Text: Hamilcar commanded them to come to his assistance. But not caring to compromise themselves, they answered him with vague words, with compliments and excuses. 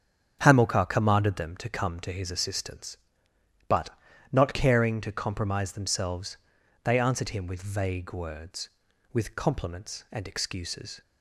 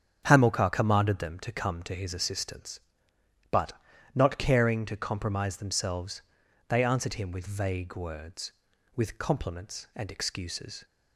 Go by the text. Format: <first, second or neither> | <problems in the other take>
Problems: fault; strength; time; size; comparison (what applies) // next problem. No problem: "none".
neither | starts louder than the rest; strong; the same in both // pauses between "But" and "not"; the same in both